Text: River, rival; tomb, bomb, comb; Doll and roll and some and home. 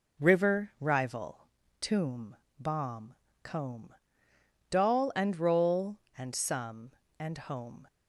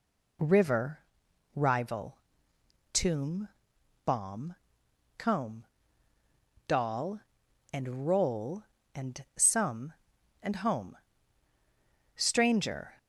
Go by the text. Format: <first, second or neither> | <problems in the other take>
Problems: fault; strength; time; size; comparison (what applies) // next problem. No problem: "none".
first | goes on to say "Stranger"; noticeable; from 12.1 s on; 0.82 s long